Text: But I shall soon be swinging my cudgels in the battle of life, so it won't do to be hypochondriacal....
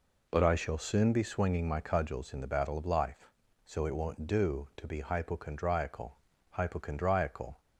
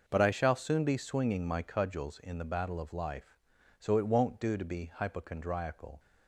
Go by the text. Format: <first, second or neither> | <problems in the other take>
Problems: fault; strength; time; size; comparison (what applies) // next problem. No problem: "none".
second | says "hypochondriacal" twice; at 6.4 s